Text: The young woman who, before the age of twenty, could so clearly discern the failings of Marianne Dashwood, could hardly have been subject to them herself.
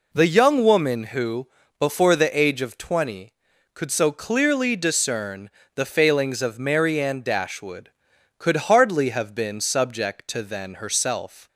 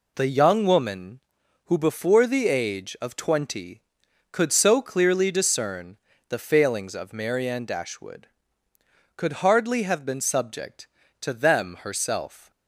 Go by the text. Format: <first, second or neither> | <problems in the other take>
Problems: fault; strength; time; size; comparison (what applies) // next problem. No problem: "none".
second | pauses between "discern" and "the"; slight; at 5.4 s; 0.26 s long; slight in the second // says "then" for "them"; at 10.4 s